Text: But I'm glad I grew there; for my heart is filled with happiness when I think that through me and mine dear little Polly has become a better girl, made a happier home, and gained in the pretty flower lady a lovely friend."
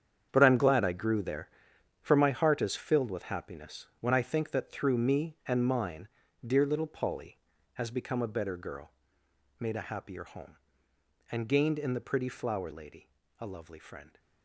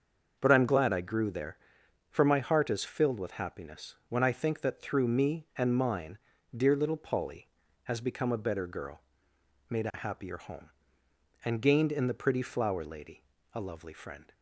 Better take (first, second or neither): second